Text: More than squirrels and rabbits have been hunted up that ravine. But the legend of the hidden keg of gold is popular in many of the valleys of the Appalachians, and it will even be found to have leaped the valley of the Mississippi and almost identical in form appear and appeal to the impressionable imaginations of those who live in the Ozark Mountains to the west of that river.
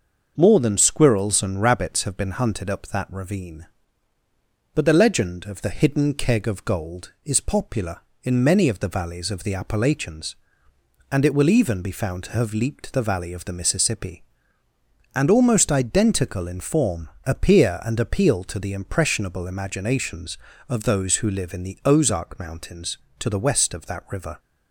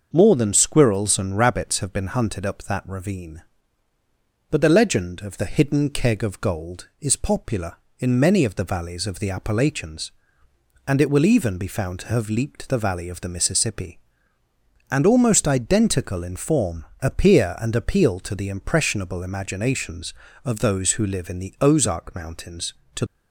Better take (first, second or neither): first